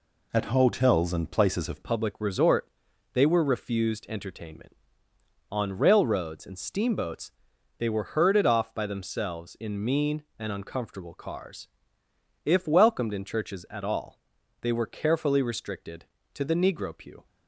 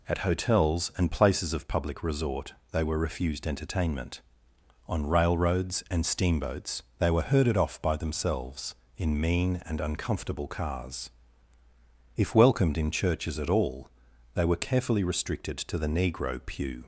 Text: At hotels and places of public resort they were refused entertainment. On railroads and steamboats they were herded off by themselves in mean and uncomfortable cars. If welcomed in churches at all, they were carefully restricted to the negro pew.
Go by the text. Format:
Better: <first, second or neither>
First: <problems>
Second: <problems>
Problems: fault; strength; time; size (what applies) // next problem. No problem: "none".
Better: second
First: changes voice at "public"; from 1.8 s on; 15.4 s long // pauses between "resort" and "they"; at 2.6 s; 0.44 s long // pauses between "steamboats" and "they"; noticeable; at 7.3 s; 0.48 s long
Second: pauses between "resort" and "they"; slight; at 2.5 s; 0.20 s long // pauses between "steamboats" and "they"; slight; at 6.8 s; 0.16 s long